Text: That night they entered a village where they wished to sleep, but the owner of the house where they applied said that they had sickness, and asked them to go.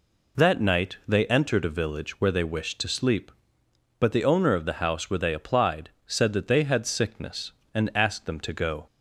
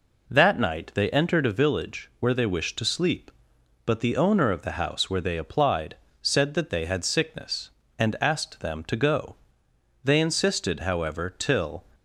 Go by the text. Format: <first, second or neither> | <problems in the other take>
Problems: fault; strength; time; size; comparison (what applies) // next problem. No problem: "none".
first | pauses between "applied" and "said"; slight; at 5.9 s; 0.26 s long; slight in the first // goes on to say "They insisted however till"; strong; from 10.0 s on; 1.8 s long